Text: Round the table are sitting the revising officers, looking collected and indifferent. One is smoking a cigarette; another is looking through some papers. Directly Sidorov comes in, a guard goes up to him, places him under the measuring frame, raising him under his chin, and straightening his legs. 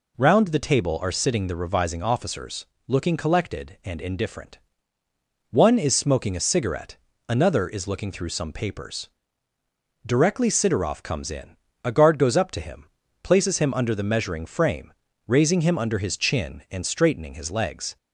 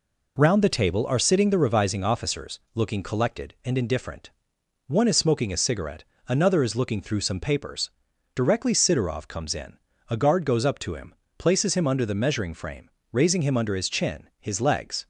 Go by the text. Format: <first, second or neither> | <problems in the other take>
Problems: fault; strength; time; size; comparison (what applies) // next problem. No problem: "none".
first | skips "and straightening"; at 14.3 s